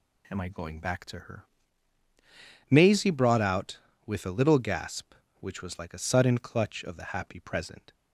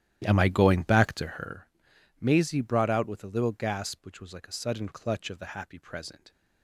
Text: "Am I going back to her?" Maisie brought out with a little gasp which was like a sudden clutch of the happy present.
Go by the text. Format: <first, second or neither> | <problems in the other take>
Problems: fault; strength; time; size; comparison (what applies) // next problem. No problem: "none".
first | starts louder than the rest; strong; until 1.5 s; 12.5 dB